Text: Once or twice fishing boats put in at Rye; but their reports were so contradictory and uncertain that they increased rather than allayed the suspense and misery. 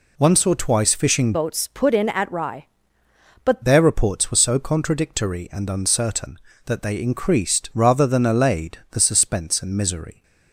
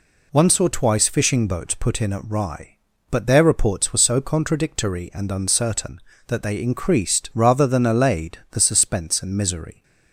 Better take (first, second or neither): second